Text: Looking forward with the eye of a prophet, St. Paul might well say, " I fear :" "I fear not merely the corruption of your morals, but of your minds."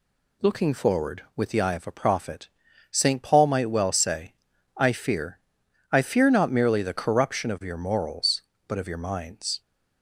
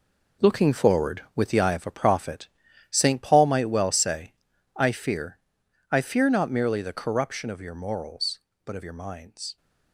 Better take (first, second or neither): first